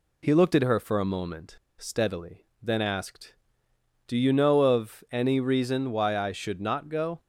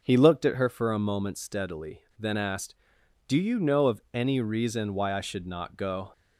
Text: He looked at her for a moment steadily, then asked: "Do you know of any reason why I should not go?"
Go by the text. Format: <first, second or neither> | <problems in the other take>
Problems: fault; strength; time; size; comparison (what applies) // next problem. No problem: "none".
second | pauses between "moment" and "steadily"; slight; at 1.5 s; 0.24 s long